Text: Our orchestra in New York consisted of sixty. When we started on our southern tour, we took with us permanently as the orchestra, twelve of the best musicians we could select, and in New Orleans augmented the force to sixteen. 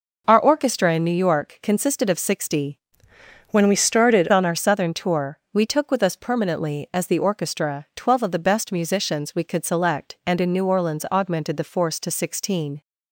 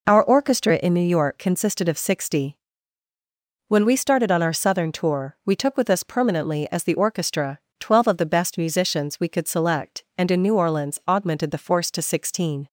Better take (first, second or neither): second